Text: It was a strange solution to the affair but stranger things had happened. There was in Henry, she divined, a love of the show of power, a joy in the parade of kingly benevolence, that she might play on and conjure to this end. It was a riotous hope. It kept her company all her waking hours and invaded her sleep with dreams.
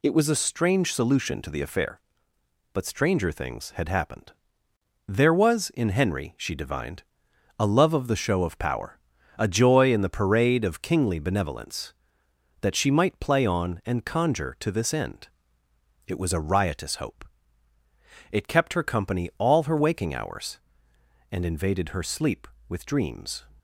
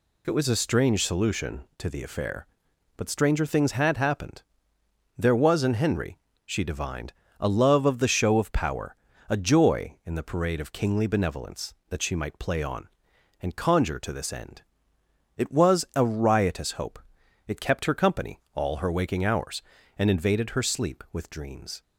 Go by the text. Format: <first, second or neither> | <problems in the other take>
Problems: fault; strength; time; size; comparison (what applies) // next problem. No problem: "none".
neither | none